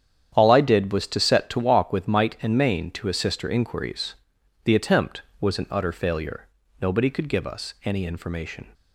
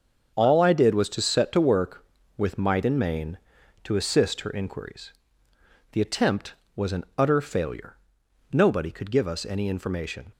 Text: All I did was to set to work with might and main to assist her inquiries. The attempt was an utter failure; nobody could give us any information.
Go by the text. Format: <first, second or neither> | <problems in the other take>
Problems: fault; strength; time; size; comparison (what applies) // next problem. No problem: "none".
second | starts louder than the rest; strong; until 1.3 s; 9.5 dB; also in the second // says "walk" for "work"; at 1.5 s